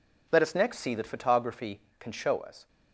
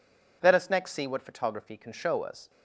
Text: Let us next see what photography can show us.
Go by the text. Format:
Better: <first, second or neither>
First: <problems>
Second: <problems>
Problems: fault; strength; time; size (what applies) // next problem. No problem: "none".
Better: second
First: says "that" for "what"; at 0.9 s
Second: none